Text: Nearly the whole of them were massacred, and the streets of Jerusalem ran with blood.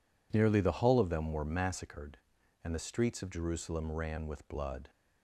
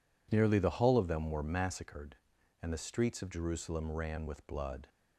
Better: neither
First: none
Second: none

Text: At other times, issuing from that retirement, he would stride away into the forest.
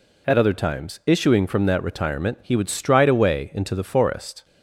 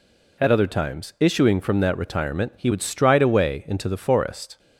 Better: neither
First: none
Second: none

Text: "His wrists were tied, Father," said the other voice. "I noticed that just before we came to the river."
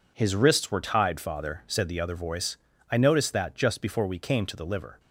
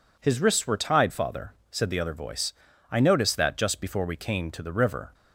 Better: second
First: says "liver" for "river"; at 4.6 s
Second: none

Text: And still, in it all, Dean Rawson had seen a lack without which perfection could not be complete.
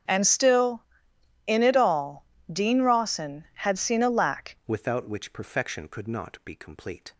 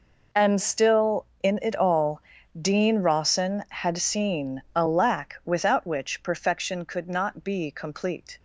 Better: second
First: starts louder than the rest; strong; until 1.7 s; 8.5 dB // changes voice at "without"; from 4.6 s on; 2.5 s long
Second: none

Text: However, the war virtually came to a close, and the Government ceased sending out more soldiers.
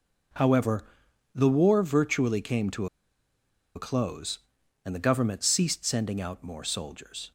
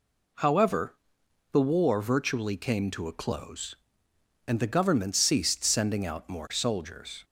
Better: second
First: pauses between "to" and "a"; noticeable; at 2.8 s; 0.89 s long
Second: none

